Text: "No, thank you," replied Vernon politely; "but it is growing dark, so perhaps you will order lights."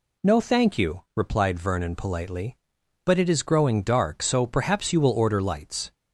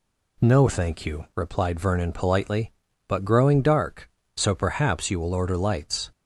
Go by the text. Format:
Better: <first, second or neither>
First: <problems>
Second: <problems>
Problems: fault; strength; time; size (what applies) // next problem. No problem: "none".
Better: first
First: none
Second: skips "it is"; at 3.2 s